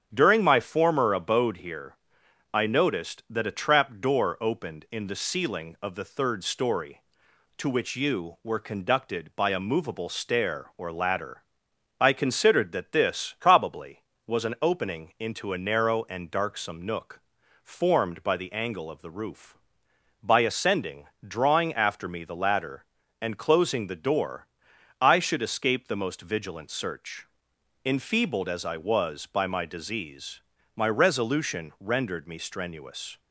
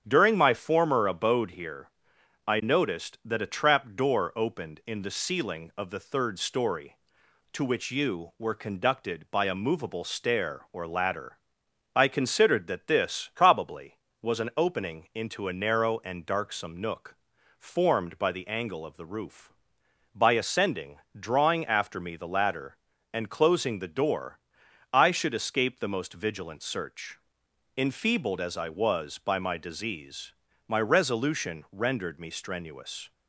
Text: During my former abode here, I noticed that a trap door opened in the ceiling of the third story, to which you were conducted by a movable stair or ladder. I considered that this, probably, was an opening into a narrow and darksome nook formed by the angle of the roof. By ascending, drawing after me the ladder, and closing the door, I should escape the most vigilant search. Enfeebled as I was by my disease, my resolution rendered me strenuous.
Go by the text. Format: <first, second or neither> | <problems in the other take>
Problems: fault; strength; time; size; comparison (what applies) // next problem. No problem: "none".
neither | starts louder than the rest; strong; the same in both // pauses between "nook" and "formed"; the same in both